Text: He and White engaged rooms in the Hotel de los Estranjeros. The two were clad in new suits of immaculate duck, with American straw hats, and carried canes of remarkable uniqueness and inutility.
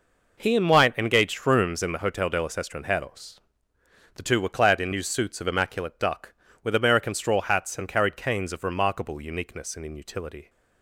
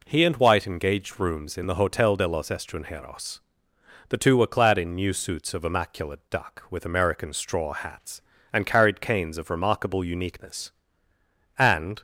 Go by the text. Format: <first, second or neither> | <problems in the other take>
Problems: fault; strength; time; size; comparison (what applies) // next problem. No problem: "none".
first | stops before "inutility"; at 11.9 s